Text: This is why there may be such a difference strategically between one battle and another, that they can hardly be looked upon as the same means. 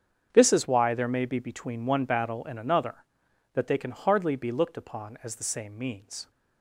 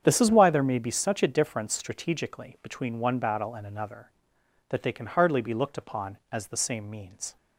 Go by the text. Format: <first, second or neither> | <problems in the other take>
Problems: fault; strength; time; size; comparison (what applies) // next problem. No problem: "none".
second | starts louder than the rest; strong; until 1.3 s; 8 dB; strong in the second // skips "such a difference strategically"; at 1.4 s